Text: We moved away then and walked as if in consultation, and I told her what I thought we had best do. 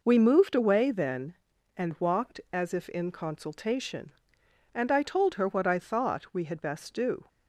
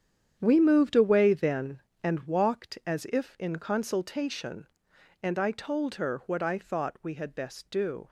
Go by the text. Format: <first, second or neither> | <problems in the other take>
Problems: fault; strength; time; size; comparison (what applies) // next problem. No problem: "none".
first | gets quieter; strong; throughout; 10.5 dB